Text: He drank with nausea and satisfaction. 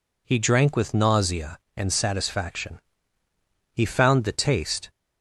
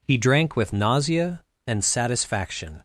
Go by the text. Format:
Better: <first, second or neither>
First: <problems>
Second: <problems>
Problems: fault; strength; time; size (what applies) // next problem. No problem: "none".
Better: second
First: goes on to say "He found the taste"; noticeable; from 3.7 s on; 1.1 s long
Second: none